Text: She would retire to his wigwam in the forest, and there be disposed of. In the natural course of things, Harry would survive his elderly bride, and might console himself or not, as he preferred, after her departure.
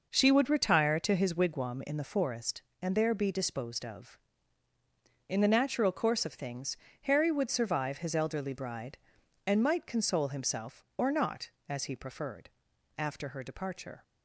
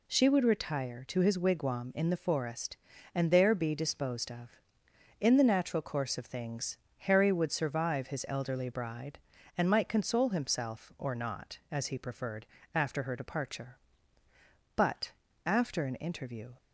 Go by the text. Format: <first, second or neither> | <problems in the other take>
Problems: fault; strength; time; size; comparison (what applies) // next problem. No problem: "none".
first | goes on to say "But after an interview"; strong; from 14.7 s on; 1.7 s long